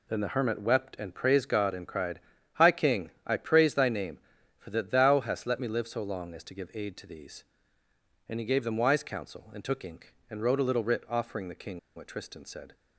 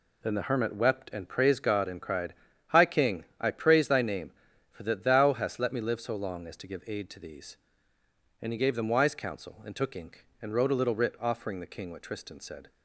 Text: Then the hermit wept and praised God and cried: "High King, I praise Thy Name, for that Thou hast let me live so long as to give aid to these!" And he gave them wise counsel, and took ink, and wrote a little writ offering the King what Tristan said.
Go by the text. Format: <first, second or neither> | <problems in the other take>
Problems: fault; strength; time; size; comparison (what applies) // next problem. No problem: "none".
second | pauses between "King" and "what"; slight; at 11.7 s; 0.17 s long